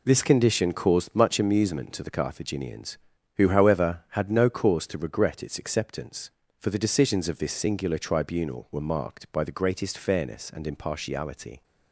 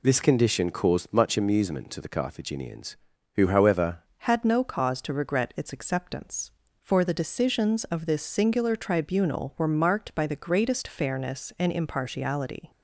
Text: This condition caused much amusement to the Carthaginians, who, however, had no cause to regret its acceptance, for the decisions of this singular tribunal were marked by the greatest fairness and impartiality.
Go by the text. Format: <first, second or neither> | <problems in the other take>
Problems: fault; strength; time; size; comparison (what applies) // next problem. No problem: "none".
first | changes voice at "had"; from 4.1 s on; 8.6 s long